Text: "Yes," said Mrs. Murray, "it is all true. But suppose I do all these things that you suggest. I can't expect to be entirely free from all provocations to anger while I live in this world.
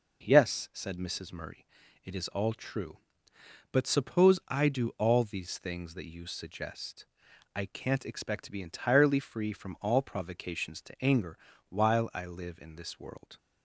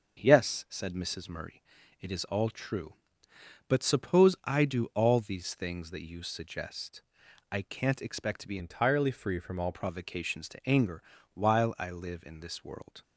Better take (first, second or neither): first